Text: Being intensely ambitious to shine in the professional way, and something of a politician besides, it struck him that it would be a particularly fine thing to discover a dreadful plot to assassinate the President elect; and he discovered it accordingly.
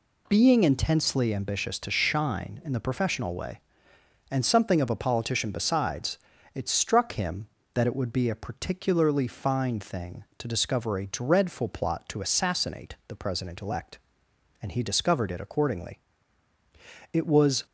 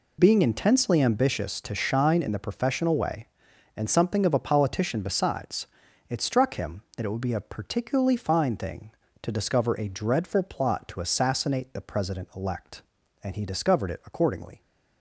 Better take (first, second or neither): second